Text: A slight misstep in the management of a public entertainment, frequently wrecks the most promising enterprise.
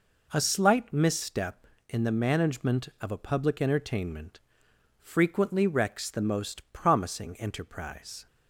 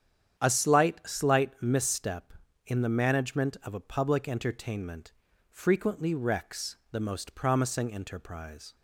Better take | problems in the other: first | starts louder than the rest; strong; until 1.4 s; 9 dB // says "slight" twice; at 1.0 s // pauses between "wrecks" and "the"; slight; at 6.7 s; 0.16 s long

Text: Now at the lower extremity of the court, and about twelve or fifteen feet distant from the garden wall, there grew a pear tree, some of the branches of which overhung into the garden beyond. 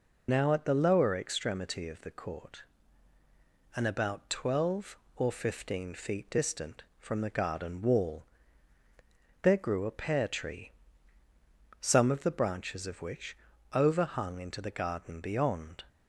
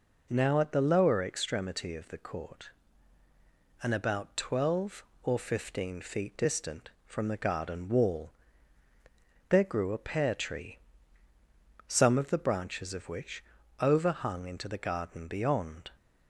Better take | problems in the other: second | loses the start of "Now"; at 0.2 s; 55 ms // pauses between "which" and "overhung"; slight; at 13.3 s; 0.36 s long; slight in the second

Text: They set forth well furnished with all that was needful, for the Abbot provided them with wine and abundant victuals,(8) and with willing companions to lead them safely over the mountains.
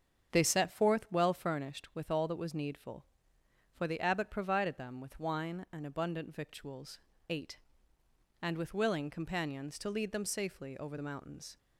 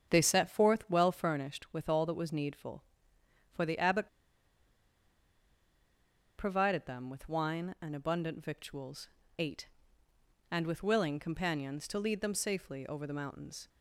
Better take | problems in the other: first | starts louder than the rest; strong; until 1.1 s; 7.5 dB; strong in the first // pauses between "Abbot" and "provided"; strong; at 4.0 s; 2.3 s long

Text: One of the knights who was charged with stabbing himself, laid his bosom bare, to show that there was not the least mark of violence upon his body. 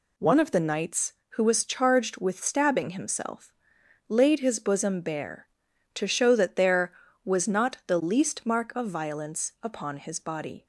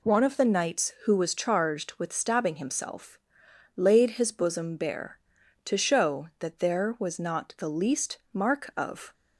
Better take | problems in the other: first | pauses between "least" and "mark"; slight; at 8.1 s; 0.16 s long // stops before "violence upon his body"; at 9.1 s

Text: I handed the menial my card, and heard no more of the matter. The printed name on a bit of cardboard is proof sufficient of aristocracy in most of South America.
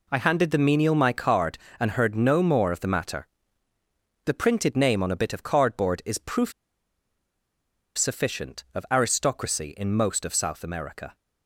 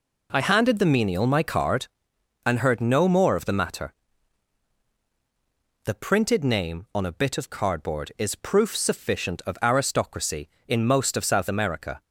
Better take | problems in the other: second | pauses between "proof" and "sufficient"; strong; at 6.5 s; 1.4 s long

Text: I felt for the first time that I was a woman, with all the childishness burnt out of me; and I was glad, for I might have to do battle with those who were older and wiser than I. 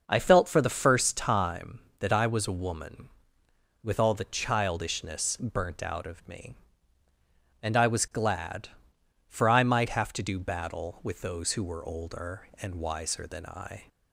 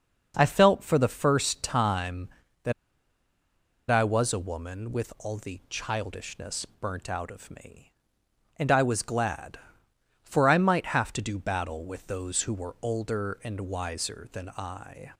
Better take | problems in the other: first | starts louder than the rest; noticeable; until 1.3 s; 6 dB // pauses between "that" and "I"; at 2.7 s; 1.1 s long

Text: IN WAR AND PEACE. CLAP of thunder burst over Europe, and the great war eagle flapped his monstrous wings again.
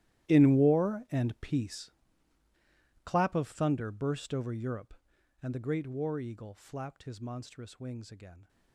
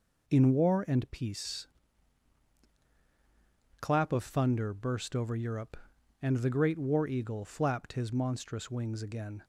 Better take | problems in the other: second | gets quieter; strong; throughout; 18 dB

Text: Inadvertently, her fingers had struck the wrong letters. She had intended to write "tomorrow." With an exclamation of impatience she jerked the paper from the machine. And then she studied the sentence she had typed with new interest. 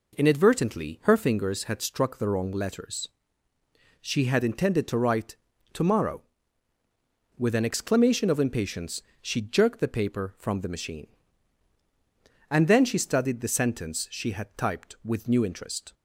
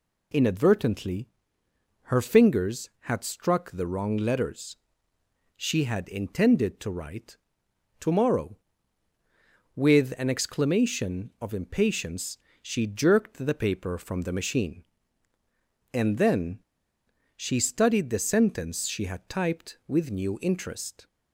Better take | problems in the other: first | pauses between "write" and "tomorrow"; noticeable; at 7.3 s; 0.64 s long; slight in the first // pauses between "impatience" and "she"; slight; at 12.3 s; 0.24 s long; slight in the first // pauses between "then" and "she"; noticeable; at 16.6 s; 0.76 s long

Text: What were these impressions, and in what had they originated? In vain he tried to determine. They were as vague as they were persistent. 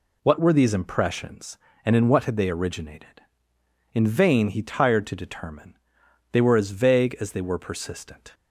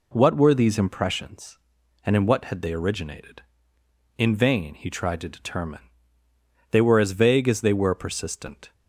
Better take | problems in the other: second | says "tired" for "tried"; at 4.6 s

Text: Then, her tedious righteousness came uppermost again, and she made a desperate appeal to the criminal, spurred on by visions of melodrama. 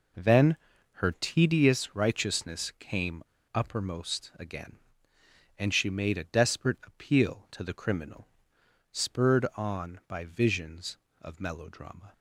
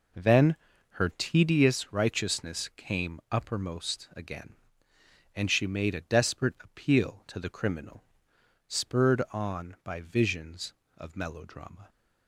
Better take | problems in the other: second | pauses between "came" and "uppermost"; slight; at 3.2 s; 0.30 s long

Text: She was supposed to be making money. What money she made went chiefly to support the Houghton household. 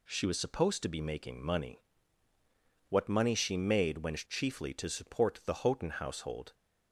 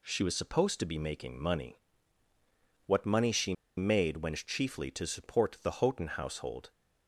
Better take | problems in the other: first | pauses between "she" and "made"; slight; at 3.5 s; 0.22 s long

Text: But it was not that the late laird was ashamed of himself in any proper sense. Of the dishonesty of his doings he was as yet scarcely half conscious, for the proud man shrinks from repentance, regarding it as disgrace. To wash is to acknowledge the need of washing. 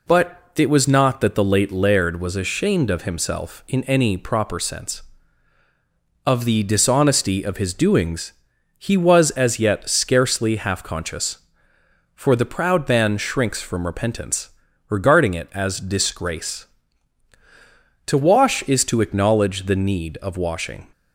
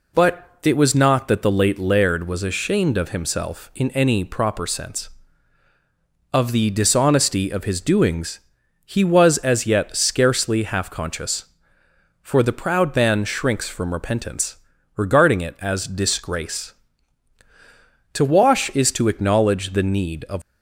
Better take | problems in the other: first | pauses between "doings" and "he"; noticeable; at 8.3 s; 0.48 s long; noticeable in the first // stops before "washing"; at 20.4 s

